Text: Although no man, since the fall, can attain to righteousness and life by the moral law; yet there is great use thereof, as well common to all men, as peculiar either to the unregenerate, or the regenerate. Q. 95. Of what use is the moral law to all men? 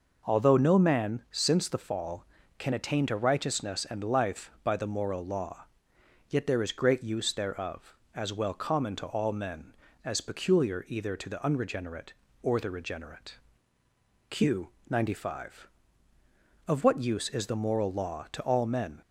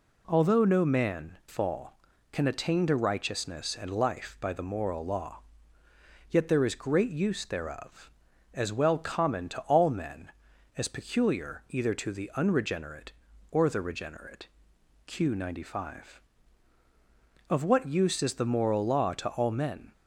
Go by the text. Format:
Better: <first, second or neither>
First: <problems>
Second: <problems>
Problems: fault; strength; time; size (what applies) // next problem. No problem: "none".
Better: first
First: none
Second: skips "since the"; at 1.4 s